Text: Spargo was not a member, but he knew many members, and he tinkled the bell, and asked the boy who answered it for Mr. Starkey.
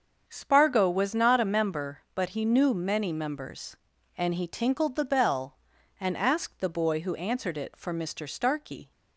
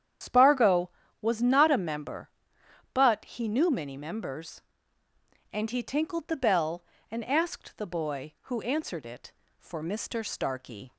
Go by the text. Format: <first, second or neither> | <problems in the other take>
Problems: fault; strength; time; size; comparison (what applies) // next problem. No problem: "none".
first | loses the start of "Spargo"; at 0.2 s; 95 ms // starts louder than the rest; strong; until 1.5 s; 9 dB; also in the first